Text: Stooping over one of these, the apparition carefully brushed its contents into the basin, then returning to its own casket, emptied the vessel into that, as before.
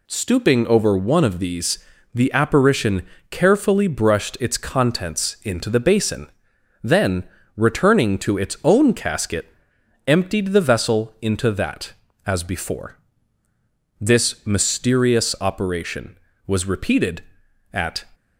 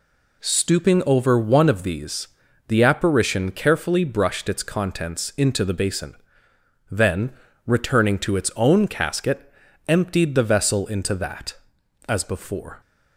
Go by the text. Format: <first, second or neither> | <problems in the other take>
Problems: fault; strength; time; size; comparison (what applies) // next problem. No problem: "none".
second | pauses between "apparition" and "carefully"; slight; at 3.0 s; 0.24 s long // pauses between "then" and "returning"; slight; at 7.2 s; 0.32 s long; slight in the second // goes on to say "This mysterious operation was repeated at"; strong; from 13.9 s on; 4.0 s long